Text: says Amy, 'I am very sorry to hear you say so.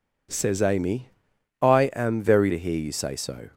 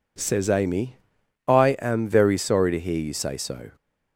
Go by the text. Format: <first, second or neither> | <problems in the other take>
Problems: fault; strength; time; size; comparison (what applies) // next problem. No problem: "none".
second | skips "sorry"; at 2.5 s